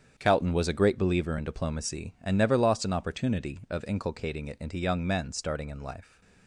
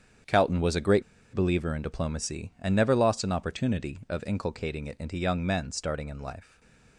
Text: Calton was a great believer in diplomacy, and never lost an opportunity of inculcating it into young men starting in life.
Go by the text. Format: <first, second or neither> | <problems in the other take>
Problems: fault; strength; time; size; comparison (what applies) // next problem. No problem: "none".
first | starts louder than the rest; strong; until 1.5 s; 8.5 dB; strong in the first // pauses between "great" and "believer"; slight; at 1.0 s; 0.30 s long // stays silent after the last word; slight; from 6.4 s on; 0.5 s long